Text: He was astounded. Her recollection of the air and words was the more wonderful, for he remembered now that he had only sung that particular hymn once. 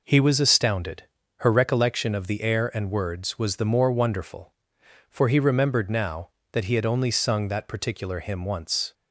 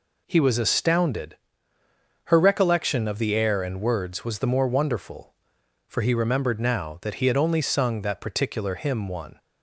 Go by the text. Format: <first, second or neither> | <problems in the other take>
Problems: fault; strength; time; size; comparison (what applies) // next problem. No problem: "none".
first | says "one" for "once"; at 9.0 s